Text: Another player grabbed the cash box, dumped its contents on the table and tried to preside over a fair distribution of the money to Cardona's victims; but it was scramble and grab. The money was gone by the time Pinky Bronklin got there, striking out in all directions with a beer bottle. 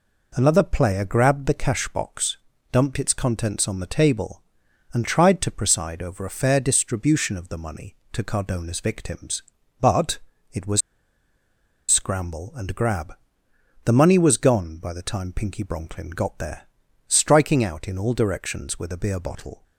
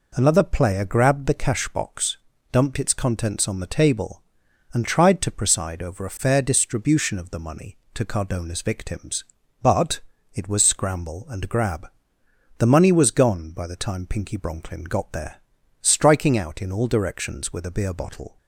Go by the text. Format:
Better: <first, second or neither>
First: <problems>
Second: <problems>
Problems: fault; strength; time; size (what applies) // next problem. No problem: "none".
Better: second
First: pauses between "but" and "it"; slight; at 10.1 s; 0.34 s long // pauses between "was" and "scramble"; at 10.8 s; 1.0 s long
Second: pauses between "but" and "it"; slight; at 9.9 s; 0.34 s long